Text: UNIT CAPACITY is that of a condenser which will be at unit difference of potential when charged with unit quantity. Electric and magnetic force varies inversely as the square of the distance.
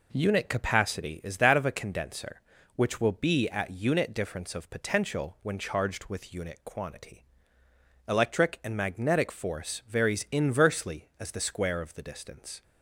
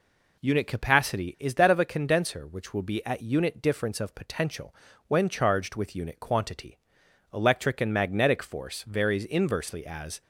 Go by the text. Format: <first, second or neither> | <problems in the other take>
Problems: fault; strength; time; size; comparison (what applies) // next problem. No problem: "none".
first | pauses between "potential" and "when"; slight; at 4.7 s; 0.34 s long // stops before "the square of the distance"; at 10.2 s